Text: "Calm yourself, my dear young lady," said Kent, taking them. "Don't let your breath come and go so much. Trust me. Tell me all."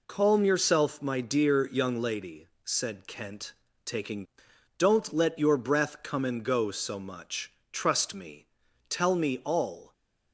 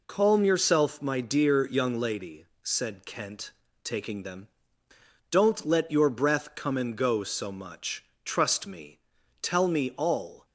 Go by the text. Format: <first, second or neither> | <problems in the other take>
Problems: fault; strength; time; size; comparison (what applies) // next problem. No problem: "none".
second | skips "them"; at 4.5 s